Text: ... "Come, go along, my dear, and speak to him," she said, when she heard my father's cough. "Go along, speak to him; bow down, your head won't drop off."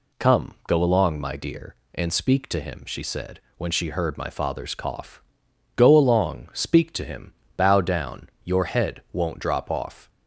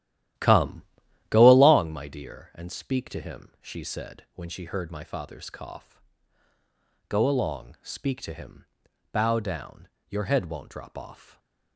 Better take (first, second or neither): first